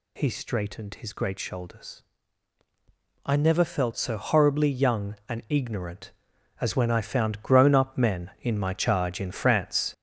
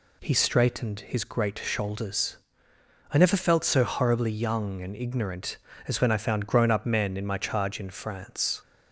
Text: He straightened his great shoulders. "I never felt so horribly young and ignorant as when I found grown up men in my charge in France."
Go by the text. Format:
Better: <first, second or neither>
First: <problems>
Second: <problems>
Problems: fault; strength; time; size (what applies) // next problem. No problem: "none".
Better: second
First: gets louder; noticeable; throughout; 5.5 dB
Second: none